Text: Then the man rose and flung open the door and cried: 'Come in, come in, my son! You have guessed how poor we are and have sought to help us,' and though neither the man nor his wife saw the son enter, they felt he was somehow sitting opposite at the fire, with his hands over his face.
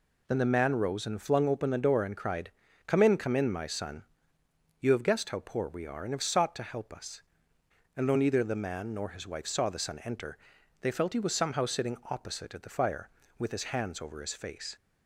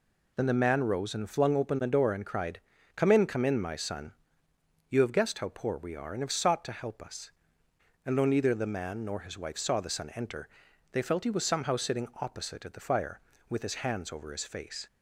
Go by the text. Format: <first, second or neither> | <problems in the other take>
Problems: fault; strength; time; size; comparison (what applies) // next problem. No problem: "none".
neither | none